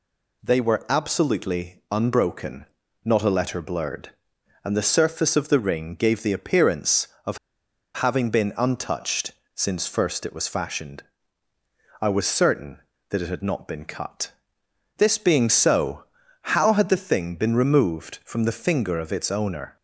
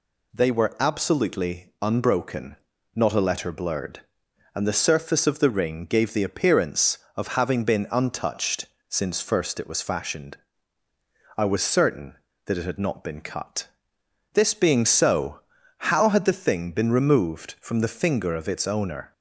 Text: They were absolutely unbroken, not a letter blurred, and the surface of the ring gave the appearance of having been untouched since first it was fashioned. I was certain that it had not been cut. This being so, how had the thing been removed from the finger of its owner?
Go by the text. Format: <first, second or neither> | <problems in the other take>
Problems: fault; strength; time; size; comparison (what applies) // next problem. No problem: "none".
second | pauses between "of" and "having"; noticeable; at 7.3 s; 0.57 s long // pauses between "untouched" and "since"; slight; at 9.3 s; 0.22 s long; slight in the second